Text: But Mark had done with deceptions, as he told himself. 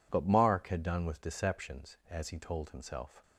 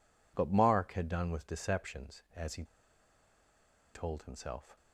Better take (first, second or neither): first